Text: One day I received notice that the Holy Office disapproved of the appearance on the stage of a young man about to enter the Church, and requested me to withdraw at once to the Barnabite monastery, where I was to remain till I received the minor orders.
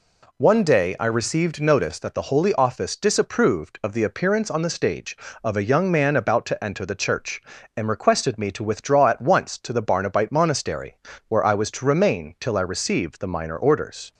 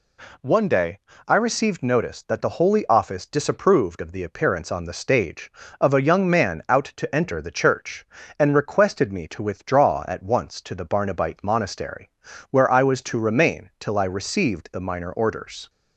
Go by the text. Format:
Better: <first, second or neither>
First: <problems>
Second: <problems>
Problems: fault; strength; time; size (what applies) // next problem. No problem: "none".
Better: first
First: none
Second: pauses between "day" and "I"; slight; at 0.9 s; 0.30 s long // says "out" for "about"; at 6.6 s